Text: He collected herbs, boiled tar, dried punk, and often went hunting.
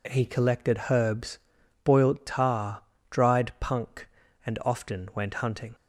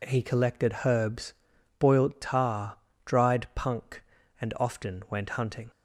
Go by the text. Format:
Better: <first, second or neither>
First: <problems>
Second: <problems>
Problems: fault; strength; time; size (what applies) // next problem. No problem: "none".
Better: neither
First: none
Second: none